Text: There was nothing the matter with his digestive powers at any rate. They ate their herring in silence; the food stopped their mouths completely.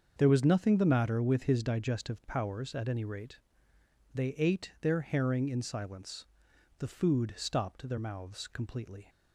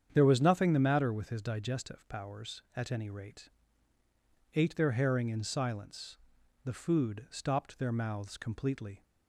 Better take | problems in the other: first | starts louder than the rest; strong; until 1.1 s; 8.5 dB; also in the first // skips "They"; at 4.0 s

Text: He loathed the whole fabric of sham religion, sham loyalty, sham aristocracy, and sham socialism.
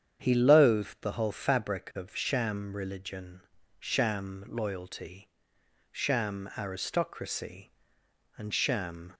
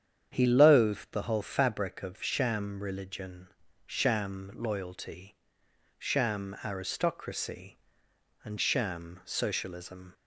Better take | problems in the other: second | starts louder than the rest; strong; until 1.2 s; 8 dB; strong in the second // stops before "socialism"; at 9.1 s

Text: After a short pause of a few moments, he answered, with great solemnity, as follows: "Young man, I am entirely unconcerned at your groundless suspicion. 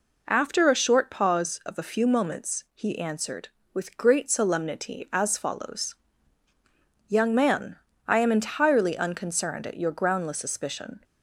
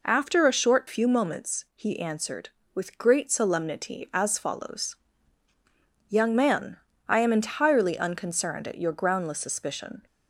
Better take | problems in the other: first | skips "pause of a"; at 0.8 s

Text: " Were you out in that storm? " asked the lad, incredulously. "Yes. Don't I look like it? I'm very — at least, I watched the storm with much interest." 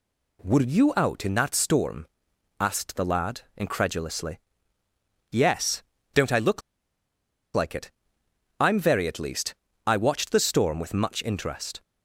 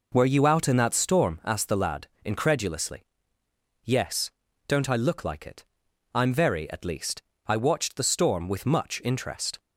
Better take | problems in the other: second | pauses between "look" and "like"; noticeable; at 6.6 s; 0.94 s long

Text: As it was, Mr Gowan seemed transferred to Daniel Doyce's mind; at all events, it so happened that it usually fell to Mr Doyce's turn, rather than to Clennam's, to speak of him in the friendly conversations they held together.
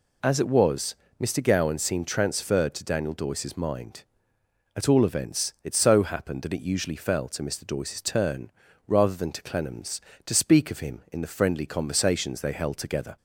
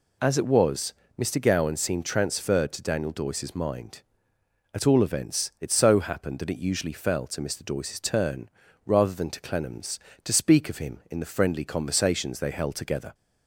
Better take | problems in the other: neither | none

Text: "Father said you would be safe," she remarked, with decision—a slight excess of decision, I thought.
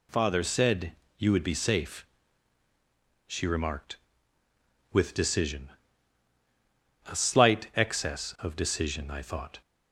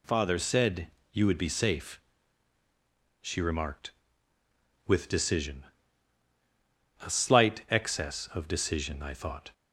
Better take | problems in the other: neither | pauses between "said" and "you"; slight; the same in both

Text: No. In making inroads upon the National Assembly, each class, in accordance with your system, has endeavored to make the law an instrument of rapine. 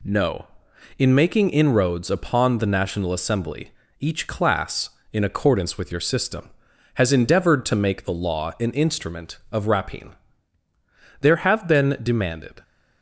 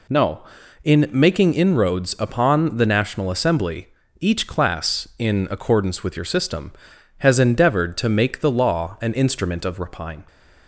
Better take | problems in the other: second | goes on to say "There have been demanded"; from 11.2 s on; 1.4 s long

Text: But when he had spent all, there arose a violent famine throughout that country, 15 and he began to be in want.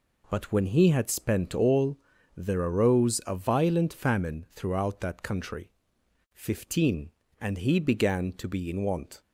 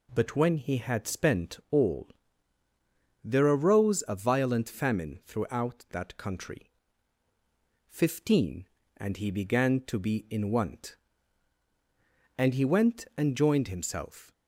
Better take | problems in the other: first | goes on to say "And he went and joined himself"; strong; from 12.3 s on; 1.9 s long

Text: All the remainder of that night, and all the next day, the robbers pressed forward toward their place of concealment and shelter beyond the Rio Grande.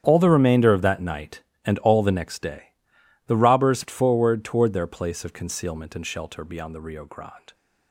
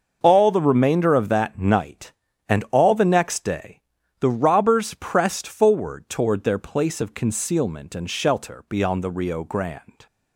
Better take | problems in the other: second | starts louder than the rest; strong; until 1.0 s; 9 dB; noticeable in the second // skips "pressed"; at 3.8 s

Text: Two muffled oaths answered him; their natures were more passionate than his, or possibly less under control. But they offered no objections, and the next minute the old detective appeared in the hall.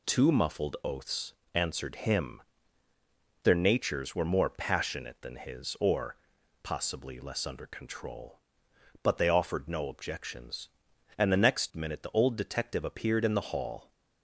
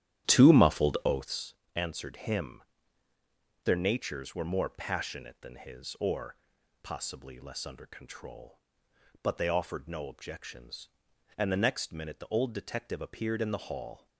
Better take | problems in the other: first | starts louder than the rest; strong; until 1.4 s; 11 dB // pauses between "oaths" and "answered"; slight; at 1.5 s; 0.22 s long; slight in the first // pauses between "or" and "possibly"; noticeable; at 6.3 s; 0.46 s long; noticeable in the first

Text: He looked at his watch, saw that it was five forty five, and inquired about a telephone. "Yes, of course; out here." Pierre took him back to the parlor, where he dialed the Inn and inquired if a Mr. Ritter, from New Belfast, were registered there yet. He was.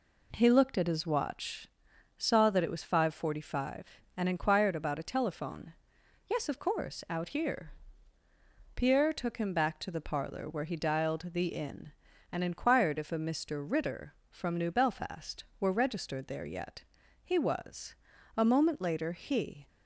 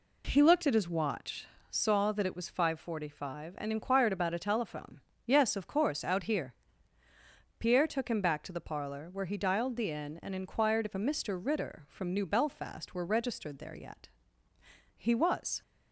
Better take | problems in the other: second | goes on to say "A moment later he"; noticeable; from 18.3 s on; 1.3 s long

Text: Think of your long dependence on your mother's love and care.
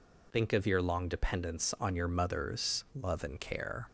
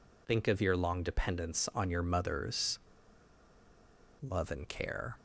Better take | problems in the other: first | pauses between "mother's" and "love"; strong; at 2.7 s; 1.4 s long

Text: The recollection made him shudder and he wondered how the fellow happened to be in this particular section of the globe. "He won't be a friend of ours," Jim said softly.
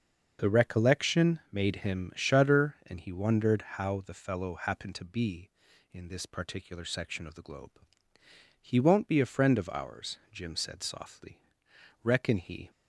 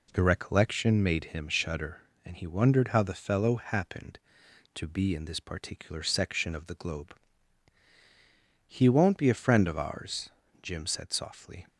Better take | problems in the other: second | starts louder than the rest; until 1.5 s; 6.5 dB // goes on to say "Reckon he"; noticeable; from 12.0 s on; 0.66 s long

